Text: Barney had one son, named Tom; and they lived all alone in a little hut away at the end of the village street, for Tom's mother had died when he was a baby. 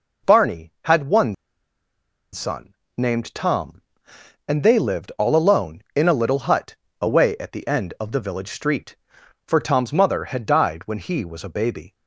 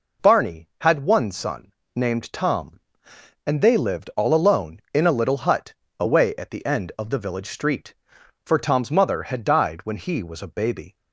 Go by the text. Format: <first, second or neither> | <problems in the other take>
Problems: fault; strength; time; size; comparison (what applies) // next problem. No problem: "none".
second | pauses between "one" and "son"; at 1.3 s; 0.98 s long // pauses between "hut" and "away"; slight; at 6.7 s; 0.26 s long; slight in the second